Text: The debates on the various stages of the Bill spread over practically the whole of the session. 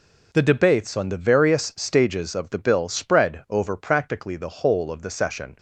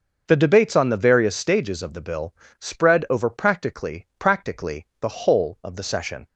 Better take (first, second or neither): first